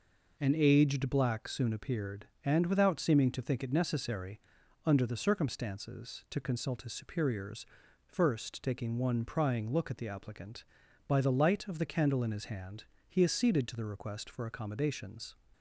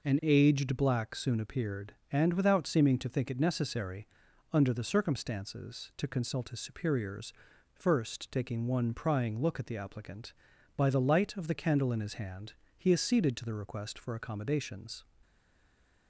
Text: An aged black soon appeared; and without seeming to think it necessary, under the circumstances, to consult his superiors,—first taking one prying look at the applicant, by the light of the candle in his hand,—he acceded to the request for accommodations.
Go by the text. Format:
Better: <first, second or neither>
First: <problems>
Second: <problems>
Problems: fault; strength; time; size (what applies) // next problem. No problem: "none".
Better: first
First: none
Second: stays silent after the last word; slight; from 15.2 s on; 0.8 s long